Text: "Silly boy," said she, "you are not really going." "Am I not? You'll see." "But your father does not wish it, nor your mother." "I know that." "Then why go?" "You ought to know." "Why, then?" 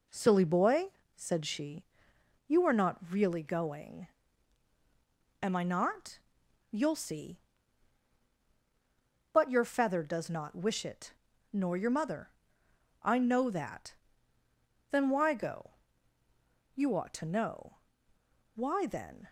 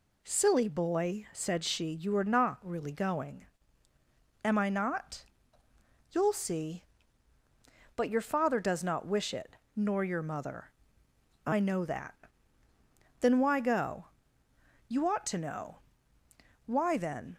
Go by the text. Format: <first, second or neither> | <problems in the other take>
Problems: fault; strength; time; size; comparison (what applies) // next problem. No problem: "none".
second | says "feather" for "father"; at 9.6 s